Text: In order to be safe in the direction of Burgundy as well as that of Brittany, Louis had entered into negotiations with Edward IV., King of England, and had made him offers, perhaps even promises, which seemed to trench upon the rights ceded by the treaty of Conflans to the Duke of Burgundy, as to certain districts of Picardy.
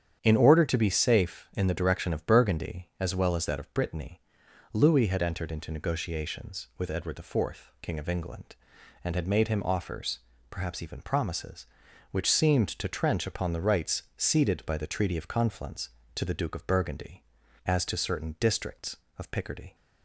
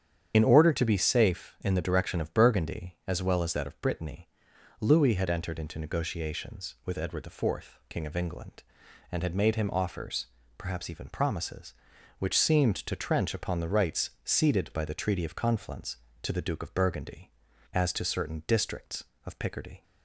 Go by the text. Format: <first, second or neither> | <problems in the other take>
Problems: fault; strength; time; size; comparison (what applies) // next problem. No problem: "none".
first | loses the start of "In"; at 0.3 s; 65 ms // starts louder than the rest; strong; until 1.3 s; 8.5 dB; strong in the first